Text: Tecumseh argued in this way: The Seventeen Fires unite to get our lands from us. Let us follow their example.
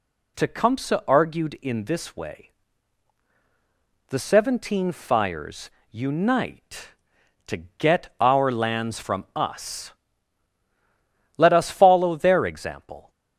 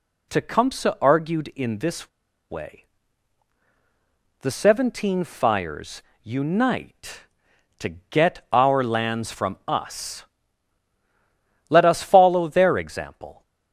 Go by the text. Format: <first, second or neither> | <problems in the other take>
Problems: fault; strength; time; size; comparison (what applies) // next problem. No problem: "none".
first | pauses between "this" and "way"; at 2.0 s; 0.42 s long // pauses between "Fires" and "unite"; slight; at 6.0 s; 0.20 s long; slight in the first // pauses between "to" and "get"; slight; at 7.8 s; 0.22 s long; slight in the first